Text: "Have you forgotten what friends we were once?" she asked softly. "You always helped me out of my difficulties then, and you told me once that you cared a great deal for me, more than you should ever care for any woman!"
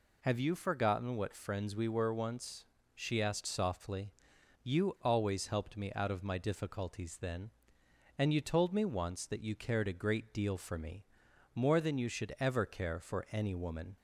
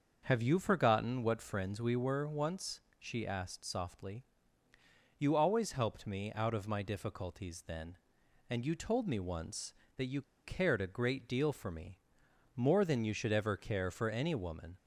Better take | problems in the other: first | starts louder than the rest; until 1.2 s; 6.5 dB // pauses between "you" and "cared"; slight; at 10.2 s; 0.22 s long

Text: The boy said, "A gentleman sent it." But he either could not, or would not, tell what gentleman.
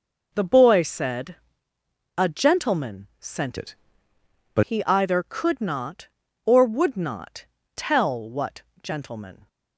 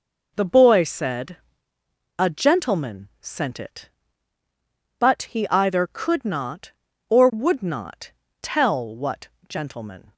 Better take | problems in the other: second | changes voice from "it" to "But"; from 3.5 to 4.6 s; 1.1 s long // pauses between "what" and "gentleman"; slight; at 8.6 s; 0.20 s long; slight in the second

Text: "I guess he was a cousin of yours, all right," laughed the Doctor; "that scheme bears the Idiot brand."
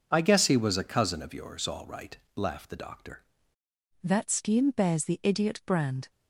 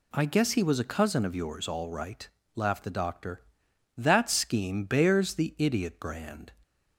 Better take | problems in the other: second | changes voice at "that"; from 4.0 s on; 2.0 s long

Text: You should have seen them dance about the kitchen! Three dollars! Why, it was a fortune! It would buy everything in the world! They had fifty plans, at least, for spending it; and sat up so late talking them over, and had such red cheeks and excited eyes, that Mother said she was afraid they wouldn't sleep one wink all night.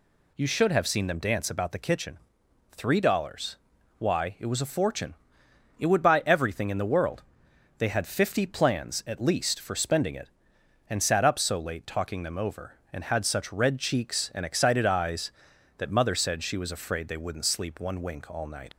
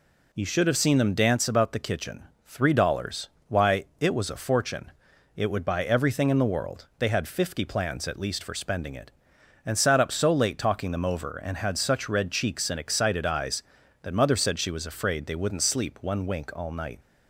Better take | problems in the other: second | leaves "night" unfinished; at 18.7 s; 75 ms

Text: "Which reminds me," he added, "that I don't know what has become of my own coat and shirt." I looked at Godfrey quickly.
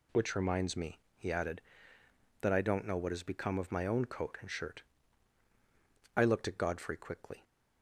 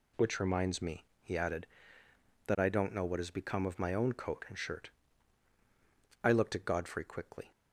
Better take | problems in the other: neither | none

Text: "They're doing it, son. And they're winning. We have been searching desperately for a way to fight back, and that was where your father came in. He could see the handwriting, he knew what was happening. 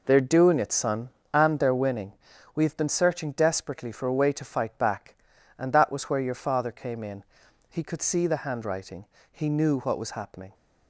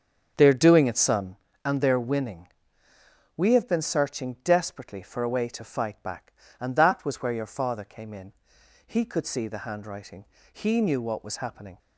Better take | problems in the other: first | starts louder than the rest; strong; until 1.5 s; 7.5 dB

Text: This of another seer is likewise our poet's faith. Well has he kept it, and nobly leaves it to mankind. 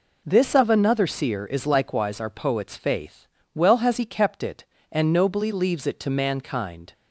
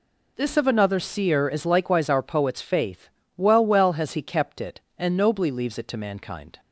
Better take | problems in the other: first | says "Well" twice; at 3.6 s

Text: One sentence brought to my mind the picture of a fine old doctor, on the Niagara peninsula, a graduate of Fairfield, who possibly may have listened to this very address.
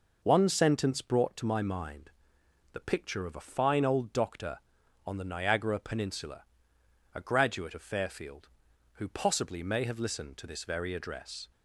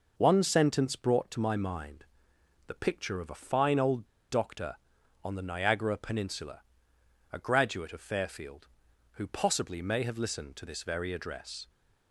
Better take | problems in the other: first | pauses between "mind" and "the"; noticeable; at 2.0 s; 0.60 s long; noticeable in the first // pauses between "old" and "doctor"; slight; at 4.0 s; 0.24 s long

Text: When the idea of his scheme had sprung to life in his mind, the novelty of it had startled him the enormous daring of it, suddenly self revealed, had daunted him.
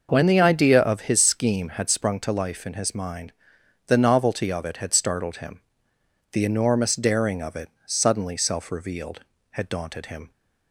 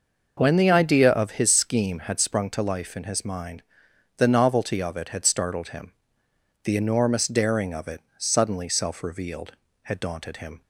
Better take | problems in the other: neither | pauses between "him" and "the"; noticeable; the same in both

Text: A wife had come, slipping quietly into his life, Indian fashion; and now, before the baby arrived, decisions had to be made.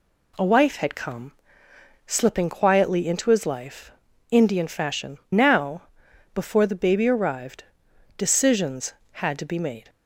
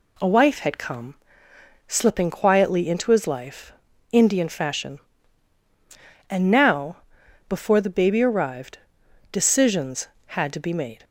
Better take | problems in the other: second | skips "and"; at 5.2 s

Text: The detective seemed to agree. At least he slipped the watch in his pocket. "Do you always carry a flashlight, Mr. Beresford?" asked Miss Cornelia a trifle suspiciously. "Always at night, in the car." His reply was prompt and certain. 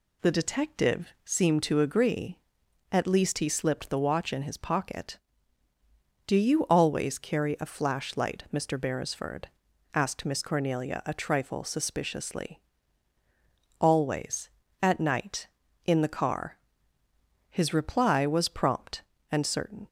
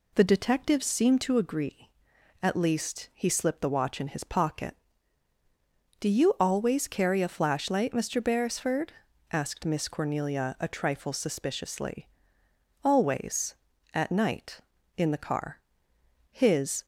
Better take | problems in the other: first | stops before "reply was prompt and certain"; at 16.8 s

